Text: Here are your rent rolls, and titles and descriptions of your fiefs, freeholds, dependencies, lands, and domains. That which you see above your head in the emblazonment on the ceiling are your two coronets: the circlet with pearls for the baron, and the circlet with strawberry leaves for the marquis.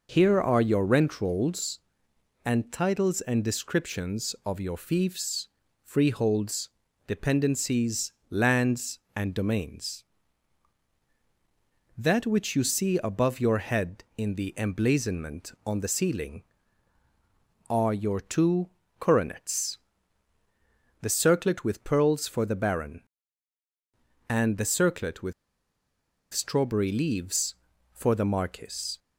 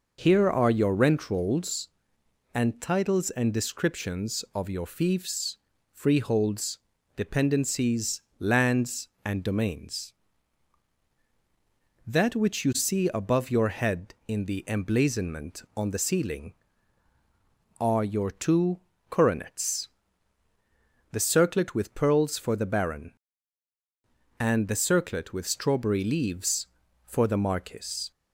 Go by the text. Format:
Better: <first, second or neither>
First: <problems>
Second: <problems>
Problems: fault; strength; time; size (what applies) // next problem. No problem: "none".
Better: second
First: pauses between "two" and "coronets"; slight; at 18.6 s; 0.30 s long // pauses between "with" and "strawberry"; at 25.3 s; 1.0 s long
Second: pauses between "two" and "coronets"; slight; at 18.7 s; 0.30 s long